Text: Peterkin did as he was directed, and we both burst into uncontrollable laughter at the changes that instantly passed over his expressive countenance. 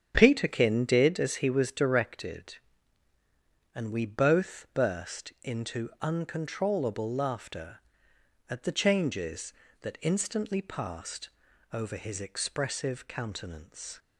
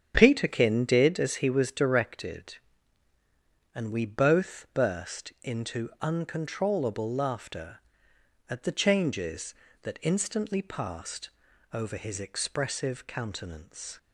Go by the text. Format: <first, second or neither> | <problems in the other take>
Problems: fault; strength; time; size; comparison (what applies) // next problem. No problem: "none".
neither | starts louder than the rest; strong; the same in both // pauses between "passed" and "over"; the same in both